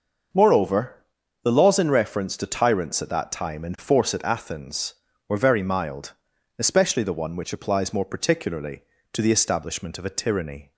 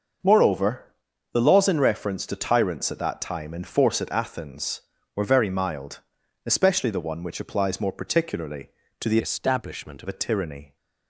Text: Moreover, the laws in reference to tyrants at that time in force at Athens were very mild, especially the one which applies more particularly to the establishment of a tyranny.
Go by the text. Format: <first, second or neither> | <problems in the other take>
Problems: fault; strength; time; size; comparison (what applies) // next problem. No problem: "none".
first | starts louder than the rest; until 1.7 s; 6 dB; also in the first // changes voice from "establishment" to "of"; from 9.2 to 10.0 s; 0.8 s long